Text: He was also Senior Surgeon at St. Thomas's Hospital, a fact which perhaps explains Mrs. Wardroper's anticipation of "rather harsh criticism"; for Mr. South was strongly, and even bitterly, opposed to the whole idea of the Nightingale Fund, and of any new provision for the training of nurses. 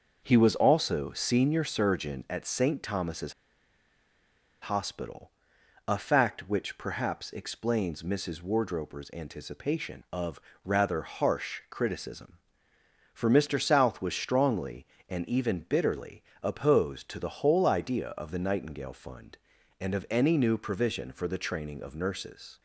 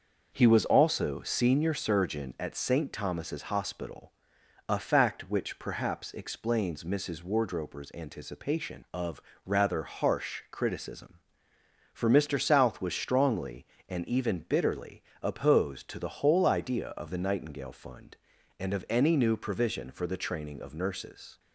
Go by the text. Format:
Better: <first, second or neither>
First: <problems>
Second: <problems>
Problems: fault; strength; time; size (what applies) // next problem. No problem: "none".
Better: second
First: starts louder than the rest; noticeable; until 1.2 s; 6 dB // pauses between "Thomas's" and "Hospital"; strong; at 3.3 s; 1.2 s long // pauses between "of" and "rather"; slight; at 10.4 s; 0.24 s long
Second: starts louder than the rest; noticeable; until 1.3 s; 6 dB // pauses between "of" and "rather"; slight; at 9.2 s; 0.24 s long